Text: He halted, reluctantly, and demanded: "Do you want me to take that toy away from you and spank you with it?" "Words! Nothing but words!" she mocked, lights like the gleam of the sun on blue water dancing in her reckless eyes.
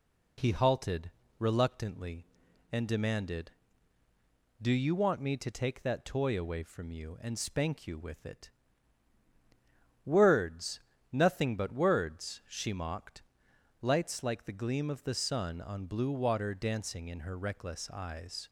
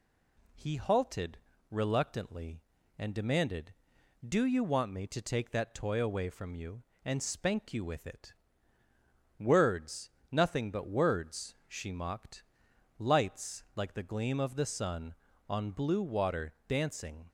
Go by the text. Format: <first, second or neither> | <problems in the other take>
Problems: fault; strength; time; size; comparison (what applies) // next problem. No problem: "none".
first | stops before "in her reckless eyes"; at 17.2 s